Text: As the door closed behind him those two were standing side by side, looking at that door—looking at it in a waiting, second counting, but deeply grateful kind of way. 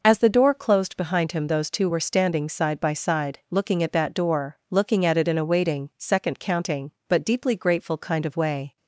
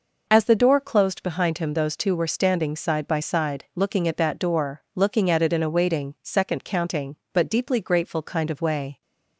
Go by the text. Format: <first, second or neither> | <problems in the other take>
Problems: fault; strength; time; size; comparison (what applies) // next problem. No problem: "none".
neither | none